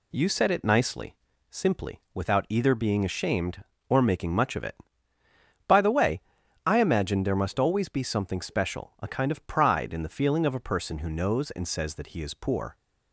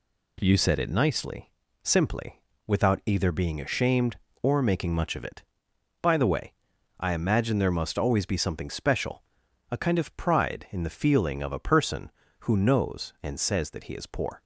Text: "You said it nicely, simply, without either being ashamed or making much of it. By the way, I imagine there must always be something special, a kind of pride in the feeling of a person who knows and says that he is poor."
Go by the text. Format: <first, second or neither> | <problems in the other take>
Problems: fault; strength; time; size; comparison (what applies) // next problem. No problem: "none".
neither | none